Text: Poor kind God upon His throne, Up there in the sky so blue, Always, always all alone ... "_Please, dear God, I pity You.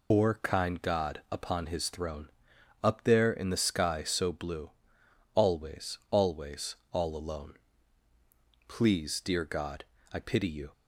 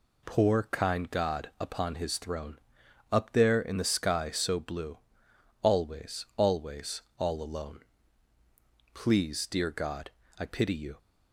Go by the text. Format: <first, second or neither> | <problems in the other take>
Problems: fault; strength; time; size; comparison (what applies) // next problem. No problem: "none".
second | loses the start of "Poor"; at 0.1 s; 140 ms // pauses between "always" and "all"; slight; at 6.7 s; 0.16 s long; slight in the second